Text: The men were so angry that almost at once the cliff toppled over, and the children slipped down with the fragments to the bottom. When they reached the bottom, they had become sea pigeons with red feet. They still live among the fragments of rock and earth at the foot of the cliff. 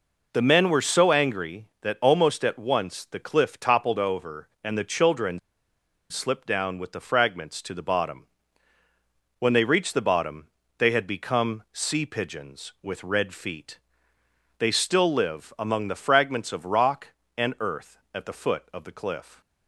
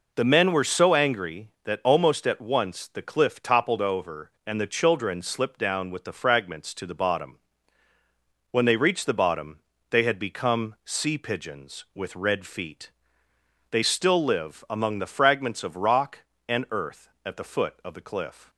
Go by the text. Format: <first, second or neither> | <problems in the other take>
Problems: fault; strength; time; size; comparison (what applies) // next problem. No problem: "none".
second | pauses between "children" and "slipped"; noticeable; at 5.3 s; 0.70 s long